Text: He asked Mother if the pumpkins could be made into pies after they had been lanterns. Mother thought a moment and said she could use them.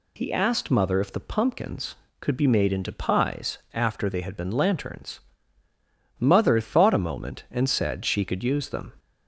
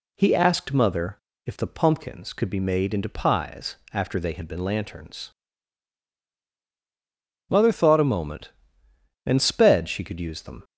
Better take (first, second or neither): first